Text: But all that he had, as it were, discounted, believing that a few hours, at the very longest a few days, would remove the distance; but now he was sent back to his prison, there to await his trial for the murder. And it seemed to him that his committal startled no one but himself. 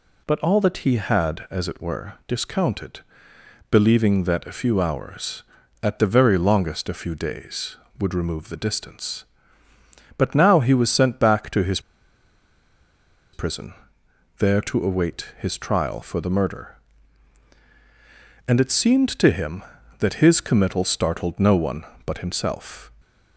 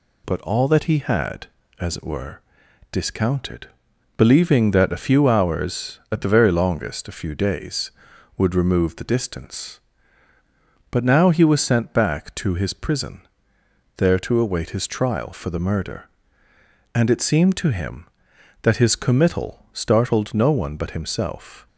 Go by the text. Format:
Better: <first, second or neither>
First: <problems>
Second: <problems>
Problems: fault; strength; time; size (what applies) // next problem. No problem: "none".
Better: second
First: pauses between "his" and "prison"; strong; at 11.7 s; 1.5 s long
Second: none